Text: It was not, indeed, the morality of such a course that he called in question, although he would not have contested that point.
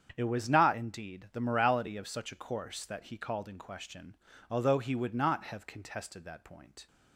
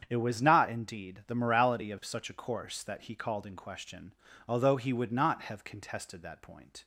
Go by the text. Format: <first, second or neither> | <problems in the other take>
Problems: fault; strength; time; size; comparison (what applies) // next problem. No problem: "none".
neither | starts louder than the rest; strong; the same in both